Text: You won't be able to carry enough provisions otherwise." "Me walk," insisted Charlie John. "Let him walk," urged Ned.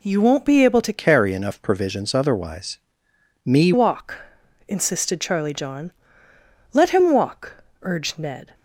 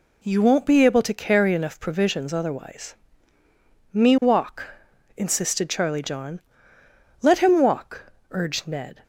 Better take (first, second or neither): second